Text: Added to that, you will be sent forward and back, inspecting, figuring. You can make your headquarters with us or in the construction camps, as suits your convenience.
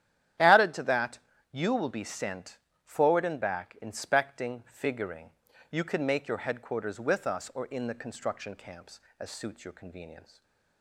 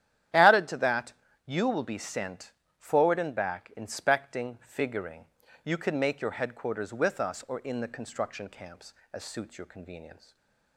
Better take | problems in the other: neither | starts louder than the rest; strong; the same in both // pauses between "sent" and "forward"; slight; the same in both // stays silent after the last word; slight; the same in both

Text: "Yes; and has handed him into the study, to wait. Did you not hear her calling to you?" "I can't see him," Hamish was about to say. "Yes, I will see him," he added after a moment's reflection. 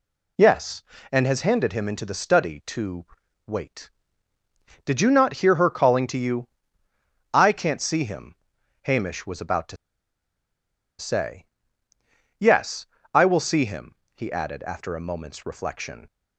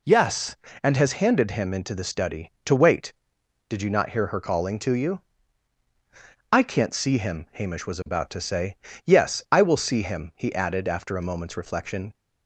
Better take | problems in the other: second | pauses between "to" and "wait"; at 3.0 s; 0.40 s long // pauses between "to" and "say"; at 9.7 s; 1.2 s long

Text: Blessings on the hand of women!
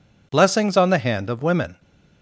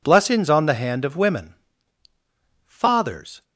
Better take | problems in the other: first | goes on to say "Fathers"; noticeable; from 2.6 s on; 0.78 s long

